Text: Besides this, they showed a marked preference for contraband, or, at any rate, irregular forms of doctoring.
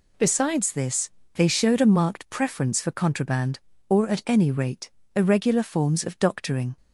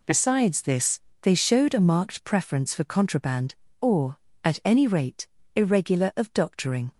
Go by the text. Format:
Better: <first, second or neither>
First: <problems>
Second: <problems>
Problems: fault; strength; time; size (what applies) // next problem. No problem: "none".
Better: first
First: none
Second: skips "forms"; at 6.1 s